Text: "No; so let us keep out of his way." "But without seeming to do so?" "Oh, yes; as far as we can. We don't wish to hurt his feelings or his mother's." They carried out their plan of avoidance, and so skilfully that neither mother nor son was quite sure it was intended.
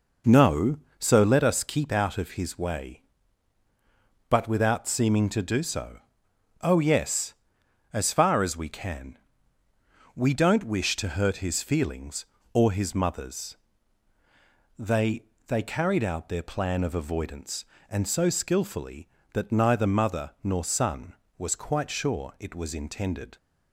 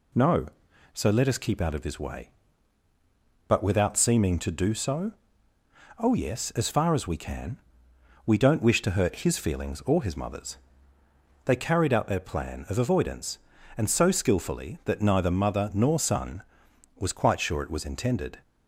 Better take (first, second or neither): second